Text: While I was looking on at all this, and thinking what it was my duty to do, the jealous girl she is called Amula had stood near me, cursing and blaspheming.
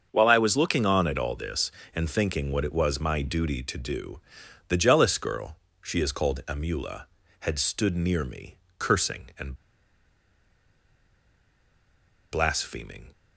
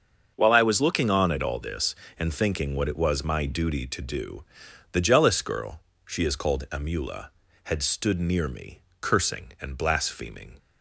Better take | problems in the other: second | starts louder than the rest; until 1.1 s; 6.5 dB; also in the second // pauses between "girl" and "she"; slight; at 5.5 s; 0.24 s long; slight in the second // pauses between "and" and "blaspheming"; strong; at 9.5 s; 2.7 s long

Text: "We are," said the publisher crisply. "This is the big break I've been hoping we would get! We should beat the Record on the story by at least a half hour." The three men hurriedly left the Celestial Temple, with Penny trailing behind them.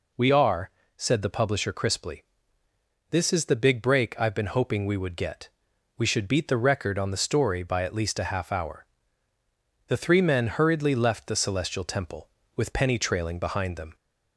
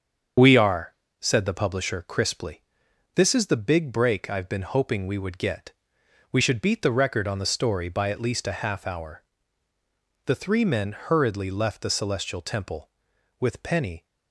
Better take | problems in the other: first | starts louder than the rest; until 1.6 s; 7 dB // stops before "trailing behind them"; at 14.0 s

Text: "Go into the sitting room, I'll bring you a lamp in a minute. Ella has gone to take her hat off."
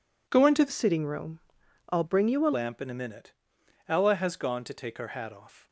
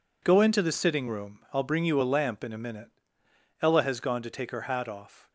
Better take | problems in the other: second | changes voice from "sitting" to "a"; from 0.6 to 2.5 s; 1.9 s long

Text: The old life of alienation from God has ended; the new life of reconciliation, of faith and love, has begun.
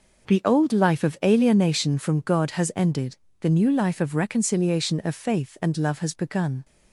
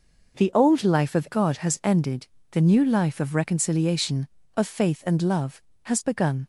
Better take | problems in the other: first | skips "alienation from"; at 1.2 s

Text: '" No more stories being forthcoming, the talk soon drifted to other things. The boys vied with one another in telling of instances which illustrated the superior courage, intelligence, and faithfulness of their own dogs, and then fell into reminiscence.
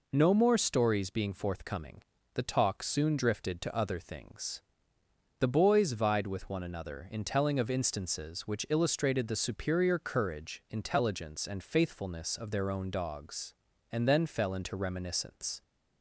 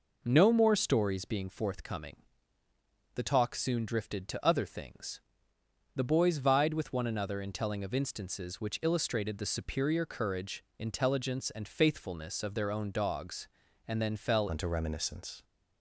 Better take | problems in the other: first | changes voice at "into"; from 14.4 s on; 1.0 s long

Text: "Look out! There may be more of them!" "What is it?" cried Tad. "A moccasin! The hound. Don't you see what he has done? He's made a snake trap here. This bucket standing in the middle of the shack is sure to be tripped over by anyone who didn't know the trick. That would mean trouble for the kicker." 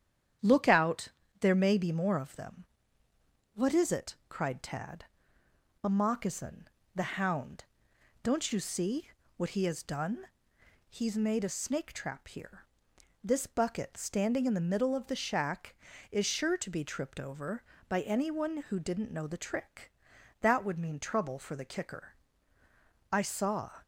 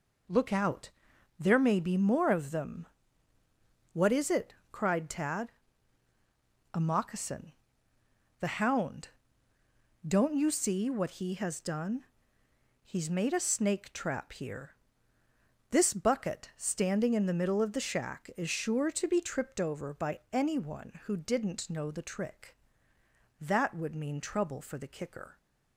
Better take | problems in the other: second | starts louder than the rest; strong; until 1.7 s; 9.5 dB // pauses between "see" and "what"; slight; at 9.0 s; 0.26 s long // goes on to say "I saw"; noticeable; from 23.1 s on; 0.70 s long

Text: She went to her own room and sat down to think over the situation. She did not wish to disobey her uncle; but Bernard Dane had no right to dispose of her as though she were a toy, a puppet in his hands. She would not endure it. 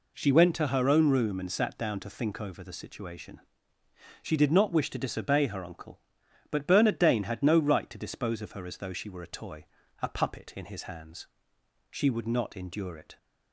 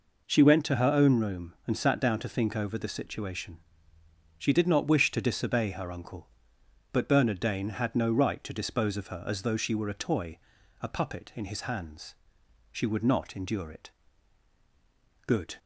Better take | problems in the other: first | goes on to say "Good"; slight; from 15.2 s on; 0.30 s long

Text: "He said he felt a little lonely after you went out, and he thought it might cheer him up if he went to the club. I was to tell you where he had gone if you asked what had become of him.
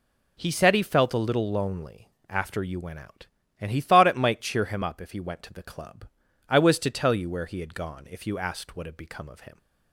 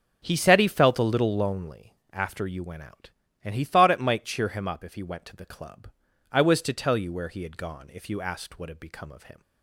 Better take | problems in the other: first | starts louder than the rest; until 1.5 s; 6 dB // pauses between "lonely" and "after"; slight; at 1.9 s; 0.18 s long; slight in the first

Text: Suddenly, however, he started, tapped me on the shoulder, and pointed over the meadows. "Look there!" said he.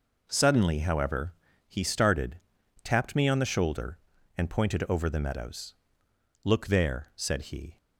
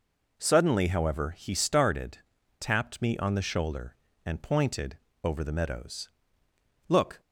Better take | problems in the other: first | pauses between "pointed" and "over"; slight; at 4.9 s; 0.24 s long // stops before "there said he"; at 7.2 s

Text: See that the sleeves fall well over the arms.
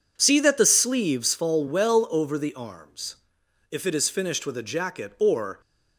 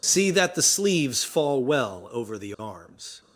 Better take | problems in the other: second | goes on to say "If it is finished with a jacket or"; strong; from 3.7 s on; 1.9 s long

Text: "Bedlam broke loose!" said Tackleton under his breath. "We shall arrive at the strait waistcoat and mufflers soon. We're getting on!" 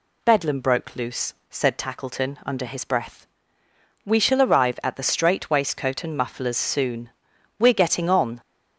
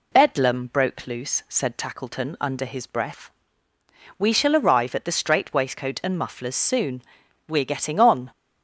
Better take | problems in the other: neither | none

